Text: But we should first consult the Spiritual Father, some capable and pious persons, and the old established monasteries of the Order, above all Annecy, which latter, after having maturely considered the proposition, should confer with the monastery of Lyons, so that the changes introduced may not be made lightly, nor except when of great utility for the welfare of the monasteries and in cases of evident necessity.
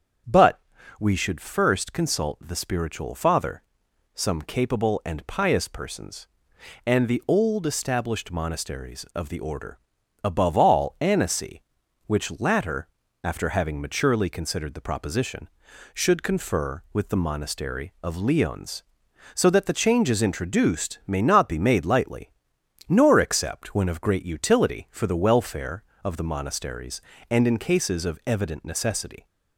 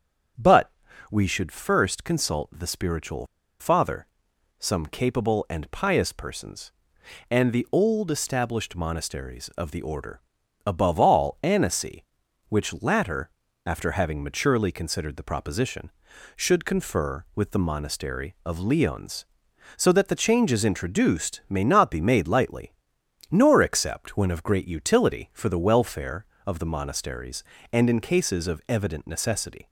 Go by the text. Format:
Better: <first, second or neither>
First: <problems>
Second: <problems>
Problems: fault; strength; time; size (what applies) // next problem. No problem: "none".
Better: first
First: starts louder than the rest; strong; until 1.6 s; 7.5 dB // pauses between "But" and "we"; at 0.6 s; 0.40 s long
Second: starts louder than the rest; strong; until 1.7 s; 7.5 dB // pauses between "But" and "we"; at 0.7 s; 0.40 s long // pauses between "Spiritual" and "Father"; slight; at 3.2 s; 0.34 s long